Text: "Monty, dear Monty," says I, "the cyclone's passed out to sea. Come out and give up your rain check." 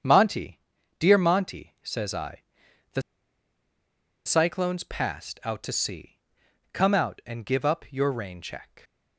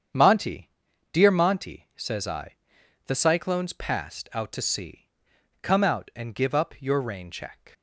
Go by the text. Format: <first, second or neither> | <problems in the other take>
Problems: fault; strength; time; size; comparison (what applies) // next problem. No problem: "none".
second | starts louder than the rest; strong; until 1.4 s; 8 dB; strong in the second // pauses between "the" and "cyclone's"; at 3.0 s; 1.2 s long